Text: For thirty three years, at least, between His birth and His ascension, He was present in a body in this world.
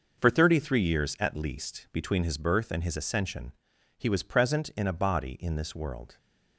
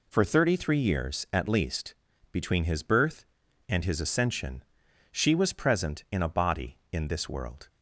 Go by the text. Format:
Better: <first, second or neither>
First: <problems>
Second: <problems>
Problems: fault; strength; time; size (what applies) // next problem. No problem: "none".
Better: first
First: none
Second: says "She" for "He"; at 5.1 s